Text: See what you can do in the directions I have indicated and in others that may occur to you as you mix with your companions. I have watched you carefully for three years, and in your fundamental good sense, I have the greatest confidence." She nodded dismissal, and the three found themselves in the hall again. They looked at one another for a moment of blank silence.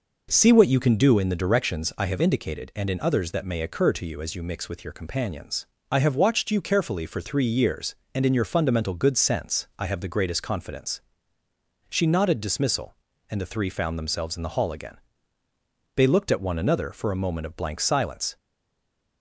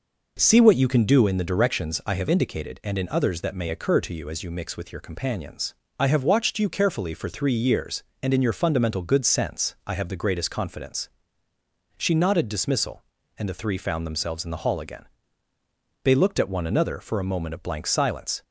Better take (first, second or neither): second